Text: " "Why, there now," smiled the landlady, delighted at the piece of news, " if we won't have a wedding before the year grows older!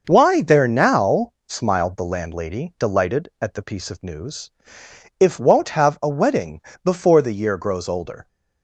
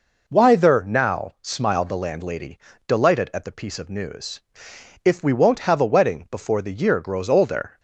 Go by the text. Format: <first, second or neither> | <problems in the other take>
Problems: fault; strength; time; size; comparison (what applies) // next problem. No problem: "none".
second | starts louder than the rest; noticeable; until 1.0 s; 6 dB // skips "we"; at 5.3 s // pauses between "wedding" and "before"; slight; at 6.6 s; 0.22 s long